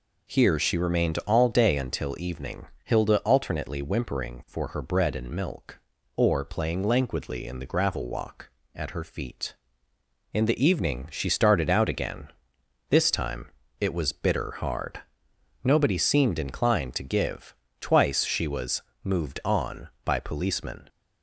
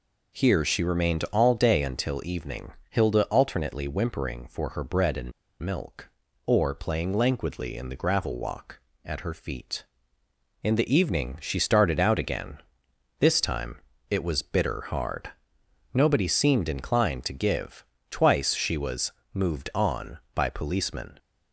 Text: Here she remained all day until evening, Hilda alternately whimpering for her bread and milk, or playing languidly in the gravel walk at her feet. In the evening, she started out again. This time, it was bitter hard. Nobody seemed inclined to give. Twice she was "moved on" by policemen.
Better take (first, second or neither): first